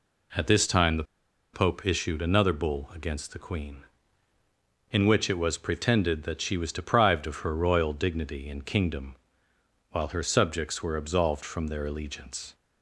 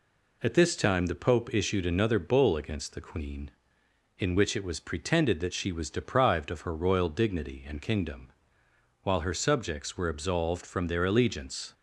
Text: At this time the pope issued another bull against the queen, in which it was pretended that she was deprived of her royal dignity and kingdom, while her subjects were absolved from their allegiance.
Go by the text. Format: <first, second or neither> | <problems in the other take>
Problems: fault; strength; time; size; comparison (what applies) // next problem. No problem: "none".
second | pauses between "the" and "pope"; noticeable; at 1.0 s; 0.50 s long